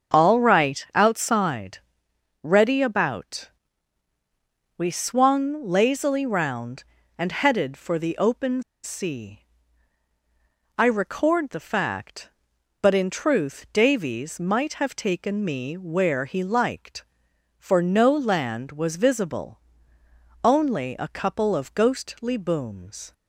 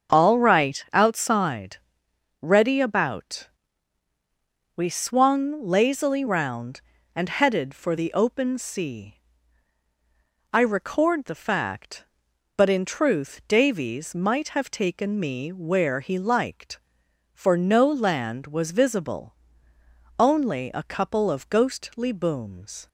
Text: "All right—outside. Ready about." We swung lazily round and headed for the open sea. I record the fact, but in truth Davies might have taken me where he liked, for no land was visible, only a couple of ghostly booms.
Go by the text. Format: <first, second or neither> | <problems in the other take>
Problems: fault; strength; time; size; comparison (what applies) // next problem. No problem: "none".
second | starts louder than the rest; until 1.2 s; 6.5 dB; also in the second // pauses between "open" and "sea"; slight; at 8.6 s; 0.21 s long